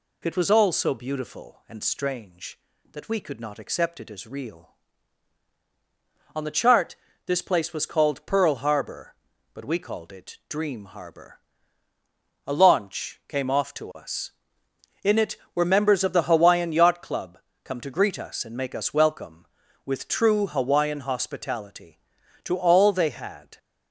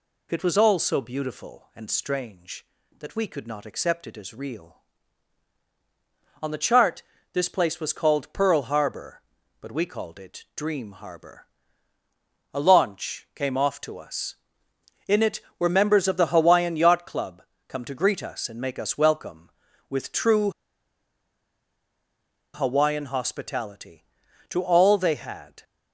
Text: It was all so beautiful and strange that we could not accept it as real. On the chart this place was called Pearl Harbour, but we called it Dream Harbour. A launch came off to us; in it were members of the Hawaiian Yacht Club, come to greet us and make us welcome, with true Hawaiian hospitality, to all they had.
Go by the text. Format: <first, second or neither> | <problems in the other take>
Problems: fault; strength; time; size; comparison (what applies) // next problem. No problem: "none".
first | pauses between "chart" and "this"; slight; at 7.0 s; 0.30 s long; slight in the first // pauses between "true" and "Hawaiian"; strong; at 20.5 s; 2.0 s long